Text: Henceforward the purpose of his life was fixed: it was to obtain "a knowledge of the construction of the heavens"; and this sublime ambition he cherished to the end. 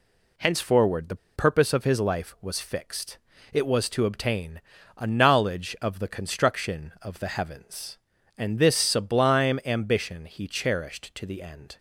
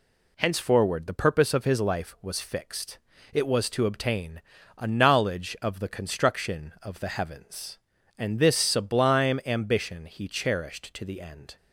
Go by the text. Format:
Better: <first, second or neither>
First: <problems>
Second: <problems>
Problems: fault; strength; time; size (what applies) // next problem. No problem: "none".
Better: second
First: pauses between "the" and "purpose"; slight; at 1.1 s; 0.19 s long // pauses between "obtain" and "a"; at 4.5 s; 0.38 s long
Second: pauses between "obtain" and "a"; at 4.3 s; 0.38 s long